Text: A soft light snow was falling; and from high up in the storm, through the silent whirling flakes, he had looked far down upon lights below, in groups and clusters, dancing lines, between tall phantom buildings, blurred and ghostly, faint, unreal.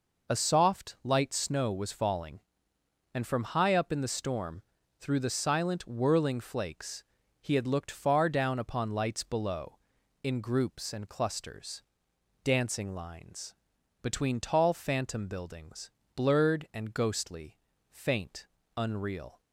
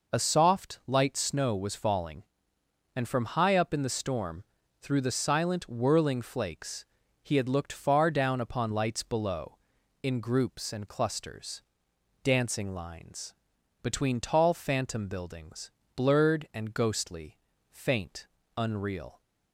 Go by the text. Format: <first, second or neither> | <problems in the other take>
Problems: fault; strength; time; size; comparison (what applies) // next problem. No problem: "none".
neither | none